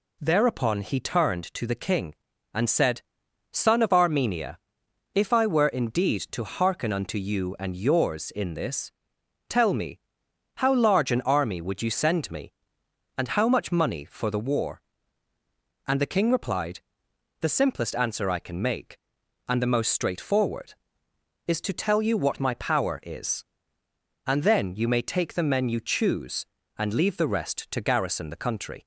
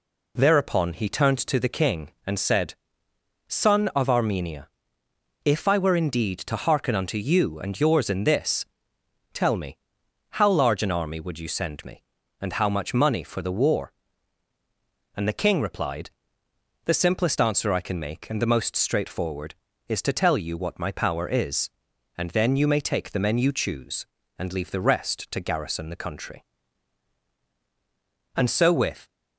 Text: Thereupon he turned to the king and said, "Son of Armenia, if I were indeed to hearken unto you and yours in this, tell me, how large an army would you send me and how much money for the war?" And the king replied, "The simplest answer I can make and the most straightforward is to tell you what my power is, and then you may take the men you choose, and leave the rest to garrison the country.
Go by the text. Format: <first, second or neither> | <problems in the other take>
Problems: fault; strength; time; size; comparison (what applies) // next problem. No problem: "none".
first | goes on to say "And so with"; noticeable; from 28.3 s on; 0.72 s long